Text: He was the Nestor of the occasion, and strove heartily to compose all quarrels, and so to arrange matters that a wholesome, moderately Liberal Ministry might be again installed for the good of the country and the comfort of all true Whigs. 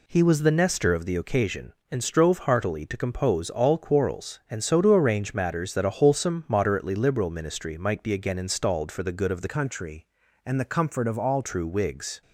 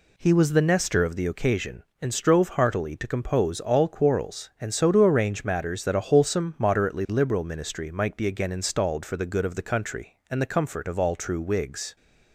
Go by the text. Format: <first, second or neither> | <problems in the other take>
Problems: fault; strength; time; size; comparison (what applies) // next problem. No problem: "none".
second | changes voice from "country" to "all"; from 9.4 to 11.4 s; 2.0 s long